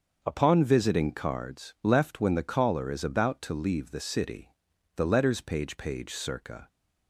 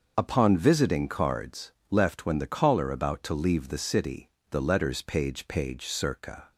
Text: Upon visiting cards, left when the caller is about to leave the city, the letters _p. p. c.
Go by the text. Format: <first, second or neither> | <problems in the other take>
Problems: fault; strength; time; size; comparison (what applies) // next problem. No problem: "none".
first | starts louder than the rest; until 1.1 s; 6 dB; also in the first // skips "is"; at 2.8 s